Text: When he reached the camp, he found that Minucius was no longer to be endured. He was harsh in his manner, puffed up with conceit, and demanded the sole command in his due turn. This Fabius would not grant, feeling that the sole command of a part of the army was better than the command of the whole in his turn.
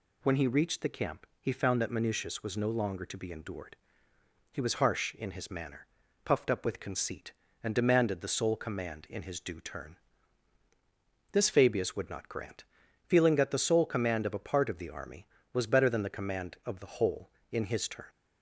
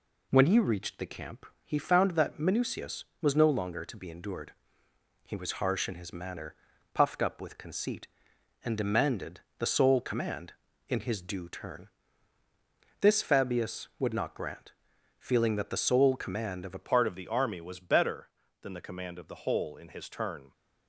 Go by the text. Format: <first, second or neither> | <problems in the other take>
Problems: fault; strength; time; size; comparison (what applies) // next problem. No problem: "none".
first | pauses between "demanded" and "the"; slight; at 9.3 s; 0.18 s long // changes voice at "part"; from 16.8 s on; 3.7 s long